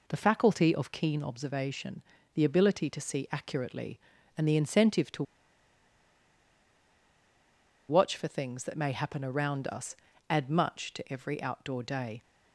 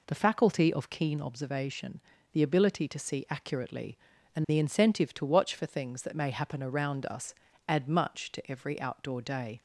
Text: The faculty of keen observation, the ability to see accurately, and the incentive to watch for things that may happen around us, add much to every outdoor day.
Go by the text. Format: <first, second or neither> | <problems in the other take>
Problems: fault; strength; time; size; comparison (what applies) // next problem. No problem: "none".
second | pauses between "to" and "watch"; strong; at 5.2 s; 2.6 s long